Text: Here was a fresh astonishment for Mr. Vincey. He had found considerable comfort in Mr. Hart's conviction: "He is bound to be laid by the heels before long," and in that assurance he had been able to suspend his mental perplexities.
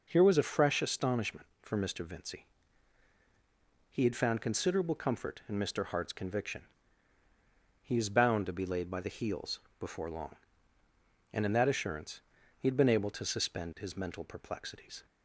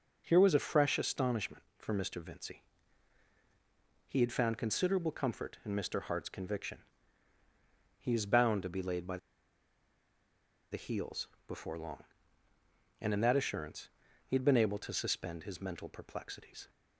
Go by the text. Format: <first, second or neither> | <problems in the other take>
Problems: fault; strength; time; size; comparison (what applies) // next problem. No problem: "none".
first | pauses between "by" and "the"; strong; at 9.1 s; 1.5 s long // pauses between "heels" and "before"; slight; at 11.2 s; 0.20 s long; slight in the first // pauses between "assurance" and "he"; slight; at 13.8 s; 0.36 s long; slight in the first